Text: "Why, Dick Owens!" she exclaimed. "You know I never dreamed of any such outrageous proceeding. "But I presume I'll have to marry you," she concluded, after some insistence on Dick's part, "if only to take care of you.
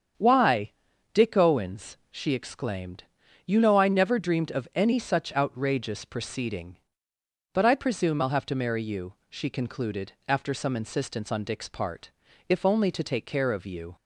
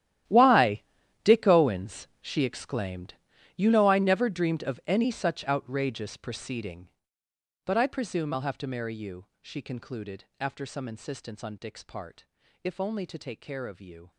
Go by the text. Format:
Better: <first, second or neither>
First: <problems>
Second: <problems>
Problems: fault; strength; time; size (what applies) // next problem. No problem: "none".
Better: first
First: starts louder than the rest; strong; until 1.5 s; 8 dB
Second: gets quieter; strong; throughout; 16.5 dB // starts louder than the rest; strong; until 1.7 s; 12.5 dB